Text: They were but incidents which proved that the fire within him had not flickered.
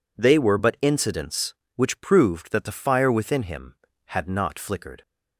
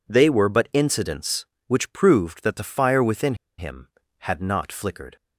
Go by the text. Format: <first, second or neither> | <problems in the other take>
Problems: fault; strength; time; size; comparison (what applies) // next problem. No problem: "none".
first | pauses between "within" and "him"; slight; at 3.3 s; 0.23 s long